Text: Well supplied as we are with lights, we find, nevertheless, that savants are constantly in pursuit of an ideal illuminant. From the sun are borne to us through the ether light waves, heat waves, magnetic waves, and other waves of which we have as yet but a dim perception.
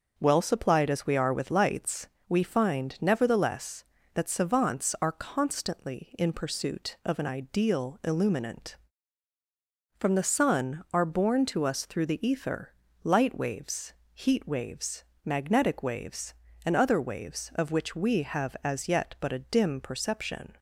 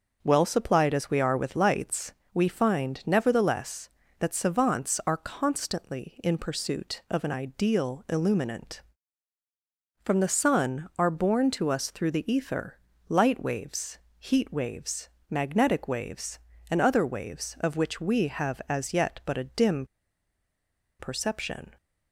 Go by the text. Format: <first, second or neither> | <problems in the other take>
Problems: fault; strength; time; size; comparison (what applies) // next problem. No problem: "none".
first | starts louder than the rest; noticeable; until 1.2 s; 6 dB; also in the first // pauses between "ether" and "light"; slight; at 12.7 s; 0.32 s long; slight in the first // pauses between "dim" and "perception"; at 19.8 s; 1.1 s long